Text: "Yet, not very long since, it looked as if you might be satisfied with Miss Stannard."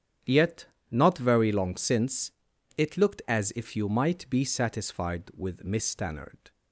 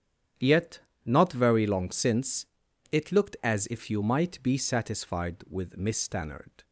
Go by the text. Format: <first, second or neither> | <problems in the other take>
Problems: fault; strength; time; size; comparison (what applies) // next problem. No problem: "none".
neither | starts louder than the rest; strong; the same in both